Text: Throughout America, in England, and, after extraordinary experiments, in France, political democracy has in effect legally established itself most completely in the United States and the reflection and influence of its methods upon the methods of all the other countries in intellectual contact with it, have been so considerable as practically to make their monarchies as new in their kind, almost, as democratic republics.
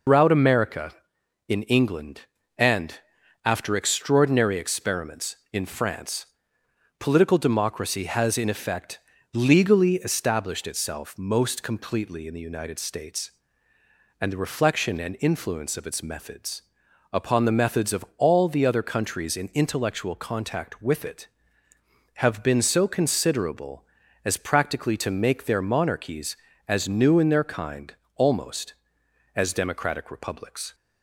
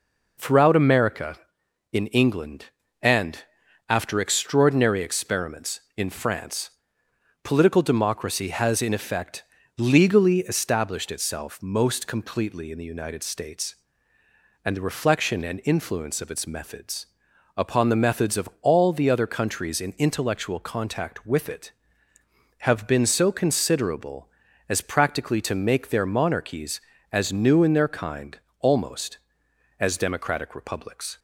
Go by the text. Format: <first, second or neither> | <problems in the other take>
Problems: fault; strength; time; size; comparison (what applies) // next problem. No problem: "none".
second | loses the start of "Throughout"; at 0.0 s; 125 ms // pauses between "effect" and "legally"; slight; at 8.9 s; 0.34 s long; slight in the second // pauses between "methods" and "upon"; noticeable; at 16.6 s; 0.50 s long; noticeable in the second